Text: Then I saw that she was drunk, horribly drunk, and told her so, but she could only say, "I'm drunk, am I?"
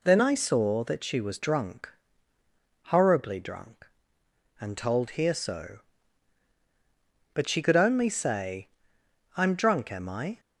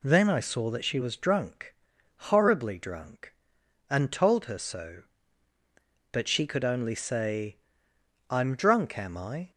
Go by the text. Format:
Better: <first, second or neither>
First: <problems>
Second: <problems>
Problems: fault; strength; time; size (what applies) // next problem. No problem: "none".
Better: second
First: says "here" for "her"; at 5.1 s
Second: none